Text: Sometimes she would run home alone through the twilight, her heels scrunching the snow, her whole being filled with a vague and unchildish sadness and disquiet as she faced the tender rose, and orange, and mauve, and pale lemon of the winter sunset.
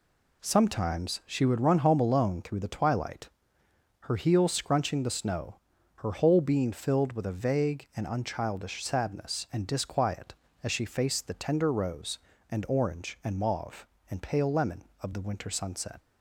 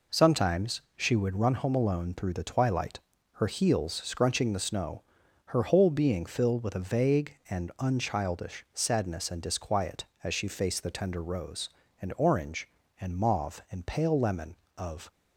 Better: first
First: none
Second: pauses between "Sometimes" and "she"; slight; at 0.8 s; 0.16 s long // stops before "the winter sunset"; at 15.1 s

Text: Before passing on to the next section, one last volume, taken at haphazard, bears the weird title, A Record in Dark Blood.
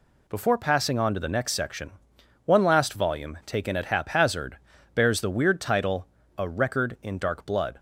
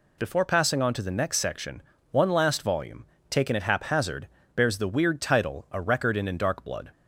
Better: first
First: none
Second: says "in" twice; at 6.2 s

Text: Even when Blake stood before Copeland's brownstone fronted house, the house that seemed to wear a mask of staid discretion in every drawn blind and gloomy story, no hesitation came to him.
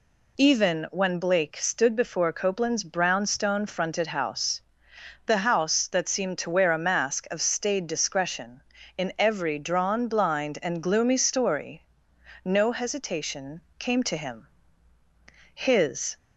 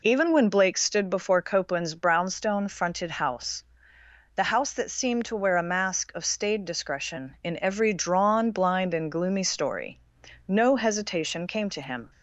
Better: second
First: pauses between "hesitation" and "came"; slight; at 13.6 s; 0.16 s long // goes on to say "His"; noticeable; from 15.5 s on; 0.64 s long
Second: none

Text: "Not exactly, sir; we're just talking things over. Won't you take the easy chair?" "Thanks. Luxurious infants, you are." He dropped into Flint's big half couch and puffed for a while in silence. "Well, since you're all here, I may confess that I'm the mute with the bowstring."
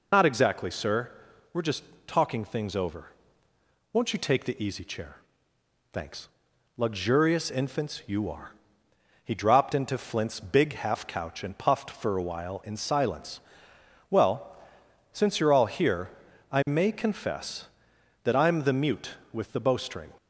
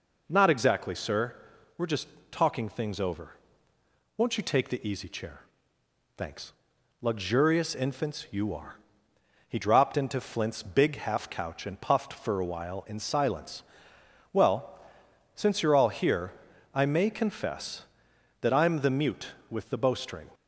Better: second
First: loses the start of "Not"; at 0.1 s; 95 ms // pauses between "just" and "talking"; slight; at 1.8 s; 0.24 s long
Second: pauses between "just" and "talking"; slight; at 2.0 s; 0.24 s long

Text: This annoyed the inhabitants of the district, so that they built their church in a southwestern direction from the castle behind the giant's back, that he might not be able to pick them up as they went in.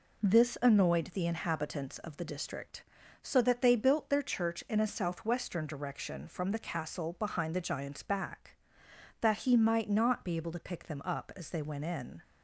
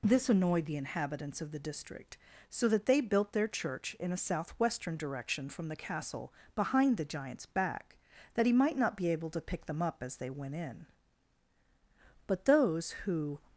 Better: first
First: none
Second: pauses between "castle" and "behind"; slight; at 6.3 s; 0.24 s long // goes on to say "But those who"; noticeable; from 12.2 s on; 1.1 s long

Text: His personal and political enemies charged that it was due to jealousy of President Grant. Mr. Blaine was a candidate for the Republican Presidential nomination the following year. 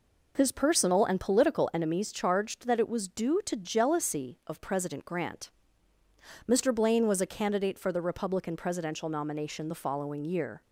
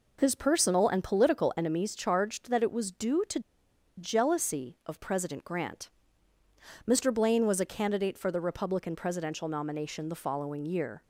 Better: first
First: none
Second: pauses between "to" and "jealousy"; noticeable; at 3.3 s; 0.57 s long

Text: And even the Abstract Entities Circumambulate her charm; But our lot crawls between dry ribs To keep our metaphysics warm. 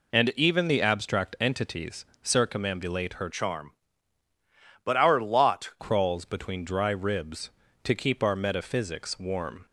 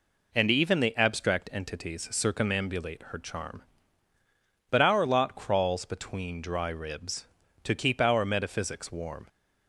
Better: second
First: pauses between "Entities" and "Circumambulate"; slight; at 2.0 s; 0.18 s long // changes voice from "charm" to "lot"; from 3.2 to 5.7 s; 2.5 s long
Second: none

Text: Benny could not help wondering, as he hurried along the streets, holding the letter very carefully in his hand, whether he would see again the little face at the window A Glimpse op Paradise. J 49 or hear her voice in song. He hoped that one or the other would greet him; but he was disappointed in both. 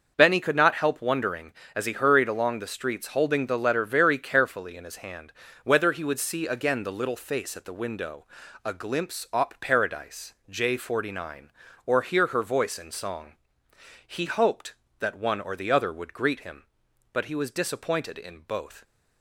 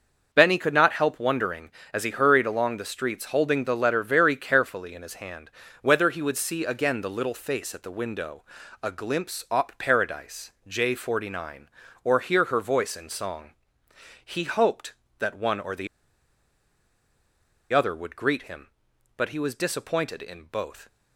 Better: first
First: starts louder than the rest; until 1.1 s; 6 dB // pauses between "window" and "A"; at 8.2 s; 0.40 s long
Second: starts louder than the rest; until 1.3 s; 6 dB // pauses between "window" and "A"; at 8.4 s; 0.40 s long // pauses between "the" and "other"; strong; at 15.8 s; 1.8 s long

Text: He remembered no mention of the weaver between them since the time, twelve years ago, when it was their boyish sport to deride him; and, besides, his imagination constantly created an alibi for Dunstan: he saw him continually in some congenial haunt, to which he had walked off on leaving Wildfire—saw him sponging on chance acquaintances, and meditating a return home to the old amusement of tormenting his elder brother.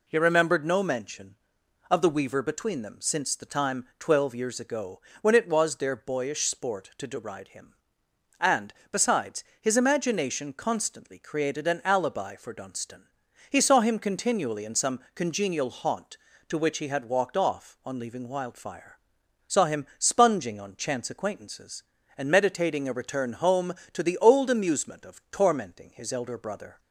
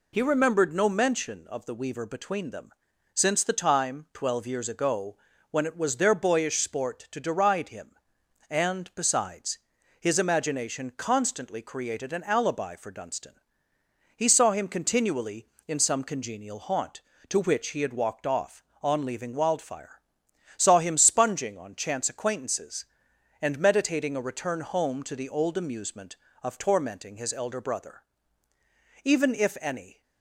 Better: first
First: none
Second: pauses between "them" and "since"; noticeable; at 2.7 s; 0.46 s long // goes on to say "Even if any"; noticeable; from 29.0 s on; 0.98 s long

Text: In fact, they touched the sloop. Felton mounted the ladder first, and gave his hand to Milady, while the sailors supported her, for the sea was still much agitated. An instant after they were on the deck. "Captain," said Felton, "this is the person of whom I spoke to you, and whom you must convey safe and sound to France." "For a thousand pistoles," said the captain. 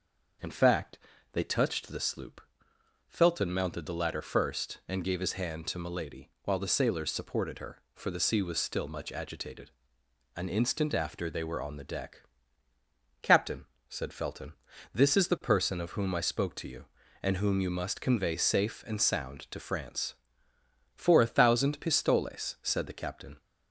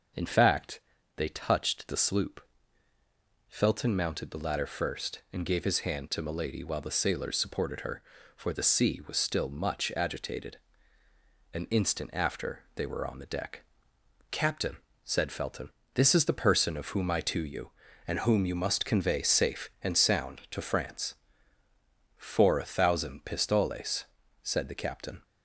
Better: first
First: starts louder than the rest; until 1.7 s; 6.5 dB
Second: starts louder than the rest; until 1.5 s; 6 dB // skips "spoke"; at 17.2 s

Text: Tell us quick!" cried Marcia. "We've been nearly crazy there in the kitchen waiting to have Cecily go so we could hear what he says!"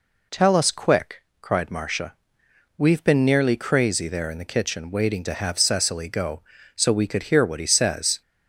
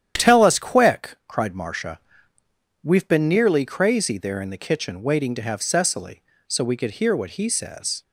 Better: first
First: none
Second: starts louder than the rest; strong; until 1.3 s; 10 dB // skips "go"; at 6.3 s

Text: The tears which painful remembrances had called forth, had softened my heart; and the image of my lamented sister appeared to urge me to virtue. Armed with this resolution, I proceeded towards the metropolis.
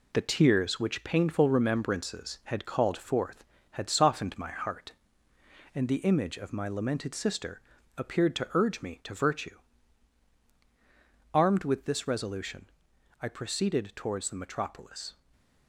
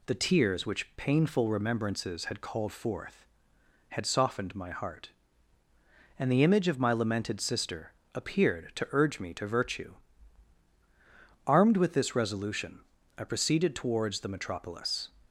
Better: second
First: gets quieter; noticeable; throughout; 6 dB // pauses between "sister" and "appeared"; slight; at 7.6 s; 0.34 s long // stays silent after the last word; slight; from 15.1 s on; 0.5 s long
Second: pauses between "sister" and "appeared"; slight; at 7.9 s; 0.20 s long

